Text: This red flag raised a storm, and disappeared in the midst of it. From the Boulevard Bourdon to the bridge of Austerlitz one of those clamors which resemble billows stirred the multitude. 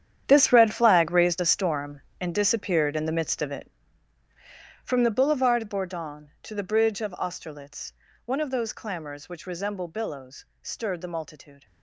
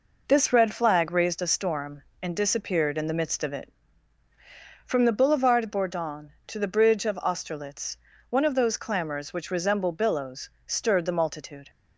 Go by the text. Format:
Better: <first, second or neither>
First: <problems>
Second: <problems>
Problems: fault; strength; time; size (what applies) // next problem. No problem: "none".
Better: second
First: gets quieter; strong; throughout; 15 dB // pauses between "Austerlitz" and "one"; slight; at 7.9 s; 0.32 s long // pauses between "billows" and "stirred"; slight; at 10.4 s; 0.16 s long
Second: pauses between "Austerlitz" and "one"; slight; at 7.9 s; 0.32 s long // pauses between "billows" and "stirred"; slight; at 10.4 s; 0.16 s long